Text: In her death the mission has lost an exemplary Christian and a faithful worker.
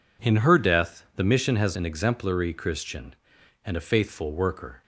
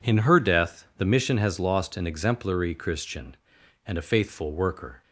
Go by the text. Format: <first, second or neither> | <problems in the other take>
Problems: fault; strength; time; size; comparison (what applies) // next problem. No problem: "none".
second | skips "lost"; at 1.7 s